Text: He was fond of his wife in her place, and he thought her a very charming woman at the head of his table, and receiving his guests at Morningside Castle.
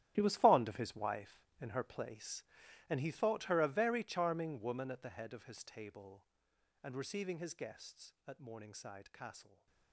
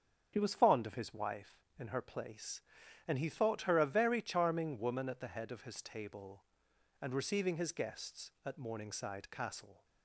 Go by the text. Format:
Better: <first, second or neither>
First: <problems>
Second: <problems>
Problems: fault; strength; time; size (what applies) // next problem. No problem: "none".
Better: second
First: gets quieter; strong; throughout; 16 dB // starts louder than the rest; strong; until 1.1 s; 11.5 dB // stays silent after the last word; slight; from 9.4 s on; 0.5 s long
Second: starts louder than the rest; until 1.3 s; 7 dB